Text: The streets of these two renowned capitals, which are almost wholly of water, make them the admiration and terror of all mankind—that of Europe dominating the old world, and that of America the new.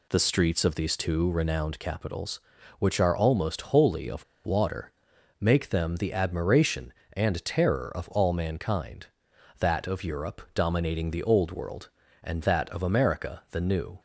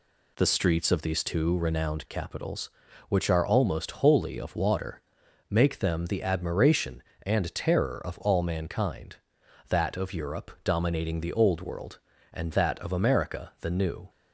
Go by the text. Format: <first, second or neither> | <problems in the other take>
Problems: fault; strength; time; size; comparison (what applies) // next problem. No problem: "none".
second | pauses between "of" and "water"; slight; at 4.2 s; 0.20 s long